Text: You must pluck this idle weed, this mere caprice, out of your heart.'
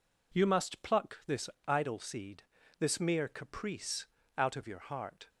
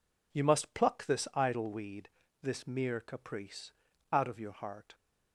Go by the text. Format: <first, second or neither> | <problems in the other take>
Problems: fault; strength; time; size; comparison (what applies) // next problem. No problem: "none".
second | pauses between "this" and "idle"; slight; at 1.4 s; 0.20 s long // says "seed" for "weed"; at 1.9 s